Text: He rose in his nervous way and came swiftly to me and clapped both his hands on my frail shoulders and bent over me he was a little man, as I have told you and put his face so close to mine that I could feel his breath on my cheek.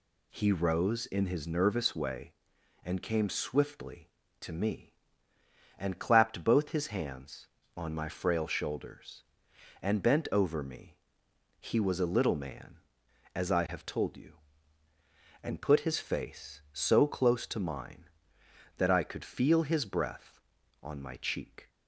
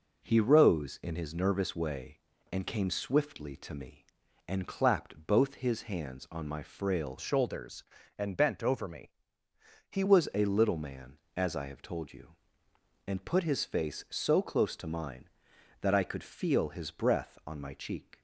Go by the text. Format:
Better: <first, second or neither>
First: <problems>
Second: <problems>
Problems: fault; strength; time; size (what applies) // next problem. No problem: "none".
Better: first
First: pauses between "me" and "he"; noticeable; at 10.9 s; 0.68 s long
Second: changes voice from "shoulders" to "he"; from 7.1 to 10.0 s; 2.9 s long // pauses between "me" and "he"; noticeable; at 9.1 s; 0.76 s long